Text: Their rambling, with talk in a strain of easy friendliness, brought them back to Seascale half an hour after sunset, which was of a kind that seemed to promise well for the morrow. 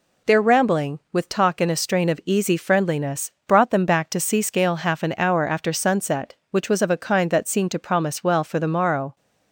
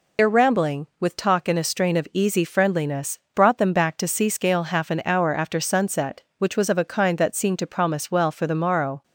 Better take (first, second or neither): first